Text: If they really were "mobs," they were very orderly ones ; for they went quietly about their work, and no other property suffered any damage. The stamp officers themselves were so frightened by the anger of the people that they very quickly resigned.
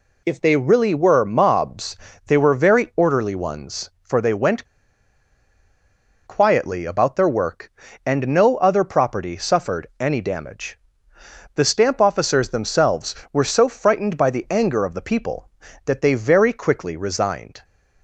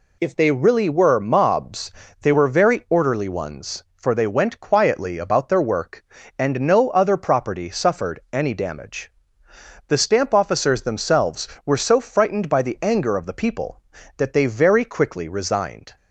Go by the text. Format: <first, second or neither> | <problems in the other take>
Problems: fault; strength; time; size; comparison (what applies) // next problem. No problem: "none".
second | pauses between "went" and "quietly"; strong; at 4.6 s; 1.6 s long